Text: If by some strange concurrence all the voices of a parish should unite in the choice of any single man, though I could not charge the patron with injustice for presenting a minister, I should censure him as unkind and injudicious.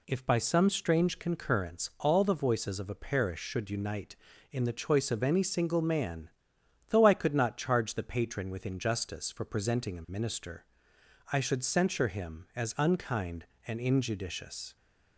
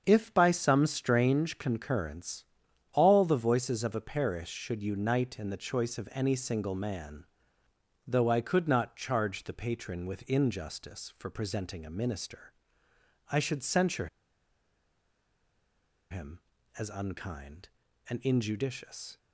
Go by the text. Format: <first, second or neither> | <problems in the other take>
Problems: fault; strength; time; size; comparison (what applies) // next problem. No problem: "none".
first | starts louder than the rest; until 1.0 s; 7 dB // pauses between "concurrence" and "all"; noticeable; at 2.4 s; 0.48 s long // pauses between "censure" and "him"; strong; at 14.0 s; 2.0 s long